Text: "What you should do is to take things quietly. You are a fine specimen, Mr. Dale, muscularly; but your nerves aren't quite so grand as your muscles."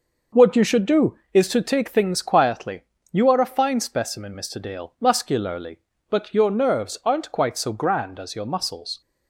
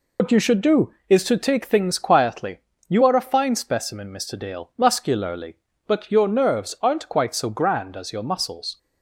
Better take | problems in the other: first | loses the start of "What"; at 0.1 s; 110 ms

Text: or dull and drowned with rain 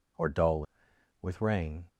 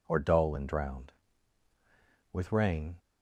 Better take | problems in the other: second | skips "and drowned"; at 0.9 s

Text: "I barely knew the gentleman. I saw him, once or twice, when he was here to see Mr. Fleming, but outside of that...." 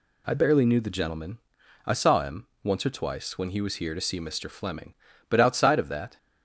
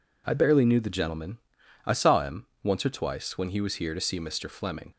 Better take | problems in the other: first | stops before "but outside of that"; at 4.9 s

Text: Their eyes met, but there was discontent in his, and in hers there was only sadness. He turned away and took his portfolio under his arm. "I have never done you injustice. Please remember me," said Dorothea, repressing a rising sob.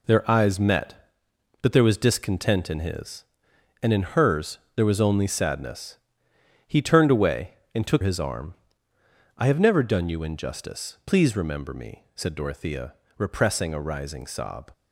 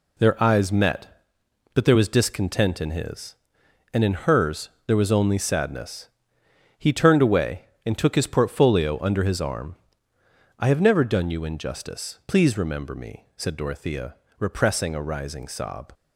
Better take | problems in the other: second | pauses between "hers" and "there"; slight; at 4.5 s; 0.16 s long; slight in the second // skips "his portfolio under"; at 8.0 s

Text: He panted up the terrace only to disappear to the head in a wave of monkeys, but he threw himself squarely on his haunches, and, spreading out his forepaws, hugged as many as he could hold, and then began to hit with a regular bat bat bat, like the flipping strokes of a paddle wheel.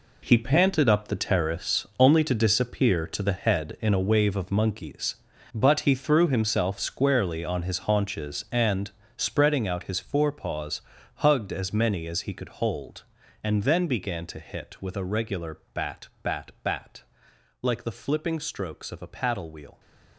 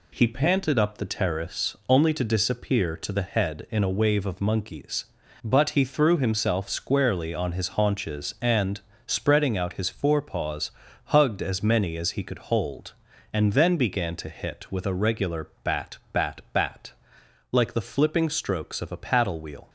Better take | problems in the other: second | gets quieter; strong; throughout; 10.5 dB // pauses between "regular" and "bat"; slight; at 15.5 s; 0.16 s long; slight in the second

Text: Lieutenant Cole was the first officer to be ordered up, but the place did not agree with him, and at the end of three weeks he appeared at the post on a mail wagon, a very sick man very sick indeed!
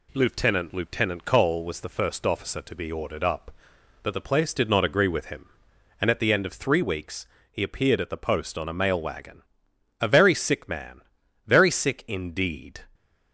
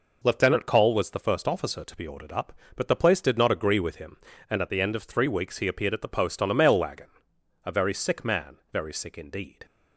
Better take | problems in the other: second | says "Lieutenant" twice; at 0.7 s // pauses between "weeks" and "he"; slight; at 7.2 s; 0.26 s long // pauses between "man" and "very"; at 11.0 s; 0.44 s long

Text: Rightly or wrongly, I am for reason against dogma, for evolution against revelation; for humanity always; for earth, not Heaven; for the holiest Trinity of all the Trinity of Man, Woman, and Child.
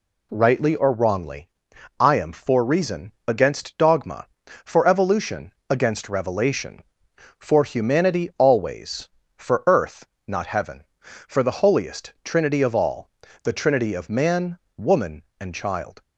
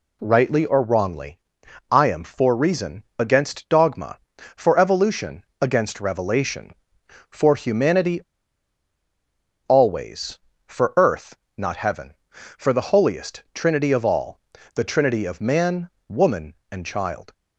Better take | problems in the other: first | pauses between "evolution" and "against"; slight; at 5.4 s; 0.16 s long; slight in the first // pauses between "humanity" and "always"; strong; at 8.2 s; 1.4 s long // pauses between "all" and "the"; slight; at 14.3 s; 0.36 s long; slight in the first

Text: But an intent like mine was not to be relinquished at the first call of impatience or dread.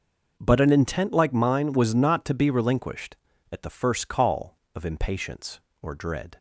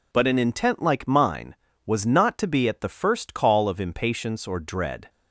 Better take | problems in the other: first | skips "relinquished"; at 2.6 s

